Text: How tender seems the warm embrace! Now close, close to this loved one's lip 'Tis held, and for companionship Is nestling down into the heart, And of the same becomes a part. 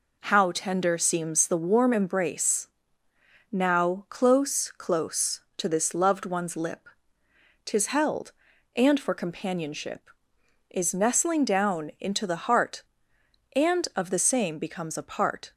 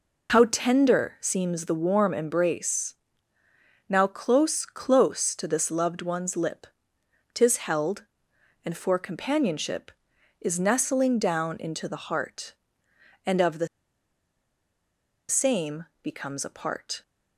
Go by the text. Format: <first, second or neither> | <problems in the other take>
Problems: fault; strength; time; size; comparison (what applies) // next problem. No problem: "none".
first | pauses between "lip" and "Tis"; noticeable; at 6.6 s; 0.66 s long; noticeable in the first // pauses between "the" and "same"; strong; at 13.6 s; 1.6 s long // pauses between "same" and "becomes"; slight; at 15.8 s; 0.18 s long